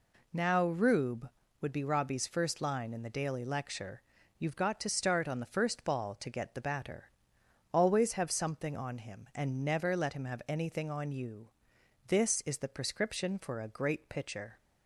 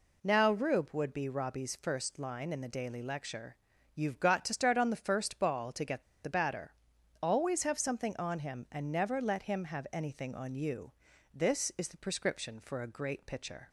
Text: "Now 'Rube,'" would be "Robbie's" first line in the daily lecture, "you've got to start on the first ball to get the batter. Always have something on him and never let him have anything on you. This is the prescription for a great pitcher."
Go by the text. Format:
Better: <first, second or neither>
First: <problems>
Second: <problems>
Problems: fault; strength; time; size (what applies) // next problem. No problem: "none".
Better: first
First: none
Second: pauses between "get" and "the"; slight; at 6.0 s; 0.19 s long